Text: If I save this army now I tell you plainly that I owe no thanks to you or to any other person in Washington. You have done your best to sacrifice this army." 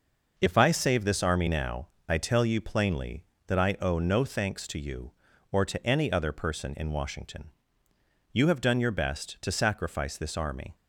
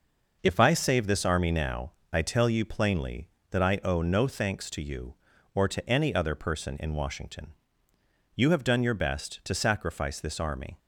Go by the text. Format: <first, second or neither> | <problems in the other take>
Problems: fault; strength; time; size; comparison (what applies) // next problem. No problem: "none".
neither | pauses between "now" and "I"; slight; the same in both